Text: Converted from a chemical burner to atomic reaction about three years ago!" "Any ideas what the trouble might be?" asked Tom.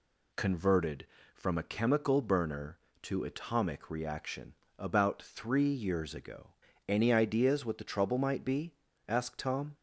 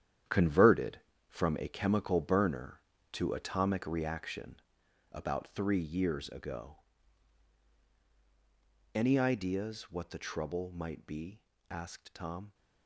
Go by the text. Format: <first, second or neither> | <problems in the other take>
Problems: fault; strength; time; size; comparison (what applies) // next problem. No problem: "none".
first | gets quieter; strong; throughout; 11.5 dB // pauses between "reaction" and "about"; noticeable; at 4.6 s; 0.52 s long; slight in the first